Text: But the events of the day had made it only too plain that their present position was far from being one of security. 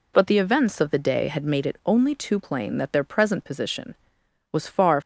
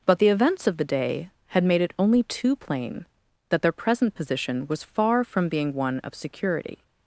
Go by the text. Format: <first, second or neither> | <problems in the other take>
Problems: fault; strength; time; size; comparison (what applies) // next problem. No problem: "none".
second | stops before "from being one of security"; at 5.0 s